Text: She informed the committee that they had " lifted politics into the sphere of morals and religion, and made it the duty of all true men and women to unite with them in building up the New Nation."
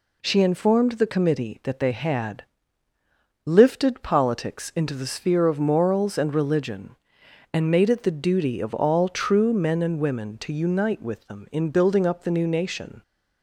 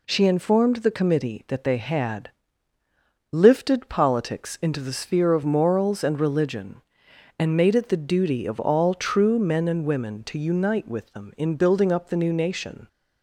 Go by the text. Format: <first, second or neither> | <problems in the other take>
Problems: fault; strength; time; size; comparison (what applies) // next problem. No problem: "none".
neither | none